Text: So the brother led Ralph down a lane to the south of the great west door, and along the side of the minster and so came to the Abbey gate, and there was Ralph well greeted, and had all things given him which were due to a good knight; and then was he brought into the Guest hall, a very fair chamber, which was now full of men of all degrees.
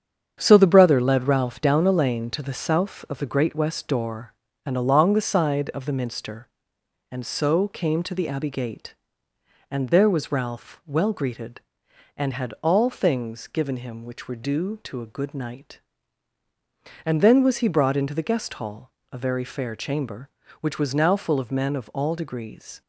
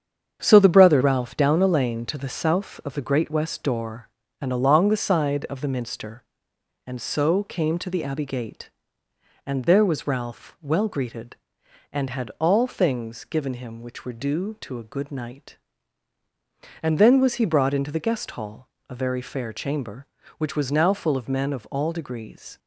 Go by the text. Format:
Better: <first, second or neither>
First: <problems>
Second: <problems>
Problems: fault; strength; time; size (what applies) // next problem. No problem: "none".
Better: first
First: starts louder than the rest; strong; until 1.4 s; 8 dB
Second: starts louder than the rest; strong; until 1.4 s; 8 dB // skips "led"; at 1.0 s